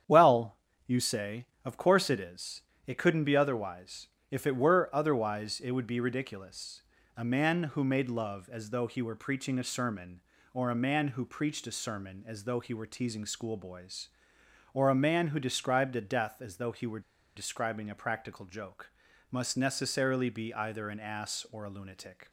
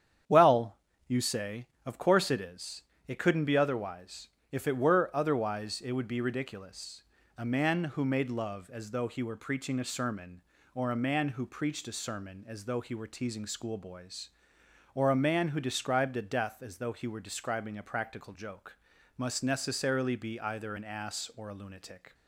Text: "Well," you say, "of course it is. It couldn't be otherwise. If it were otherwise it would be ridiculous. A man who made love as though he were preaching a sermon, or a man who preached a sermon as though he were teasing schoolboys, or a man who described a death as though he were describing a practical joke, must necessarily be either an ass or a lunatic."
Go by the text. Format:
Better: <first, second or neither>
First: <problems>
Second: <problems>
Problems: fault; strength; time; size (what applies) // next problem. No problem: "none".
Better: second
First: starts louder than the rest; strong; until 1.3 s; 9 dB // pauses between "were" and "describing"; slight; at 17.0 s; 0.35 s long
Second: starts louder than the rest; strong; until 1.5 s; 9 dB